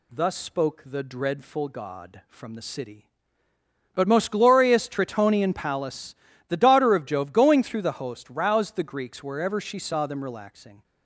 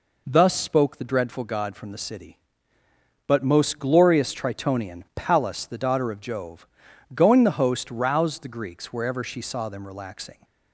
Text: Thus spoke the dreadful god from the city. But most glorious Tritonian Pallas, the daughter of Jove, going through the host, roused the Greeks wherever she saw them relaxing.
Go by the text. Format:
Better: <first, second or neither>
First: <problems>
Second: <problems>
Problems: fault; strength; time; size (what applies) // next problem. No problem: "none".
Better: first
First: none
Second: skips "through"; at 7.4 s